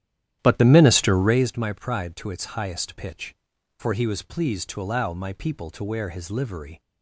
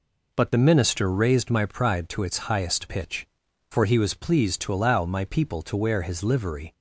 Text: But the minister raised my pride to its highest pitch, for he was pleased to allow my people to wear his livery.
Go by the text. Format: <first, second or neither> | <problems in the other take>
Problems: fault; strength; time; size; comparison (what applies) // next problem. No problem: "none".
second | starts louder than the rest; strong; until 1.6 s; 11.5 dB